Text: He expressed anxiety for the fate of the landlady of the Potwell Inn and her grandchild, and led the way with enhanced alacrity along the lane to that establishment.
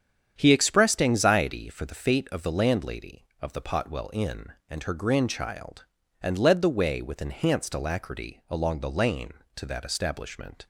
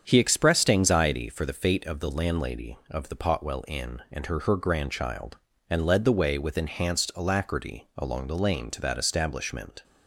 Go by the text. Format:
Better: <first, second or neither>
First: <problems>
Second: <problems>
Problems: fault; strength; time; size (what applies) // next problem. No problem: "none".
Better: first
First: starts louder than the rest; strong; until 1.3 s; 8.5 dB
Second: starts louder than the rest; strong; until 1.0 s; 7.5 dB // says "her" twice; at 4.4 s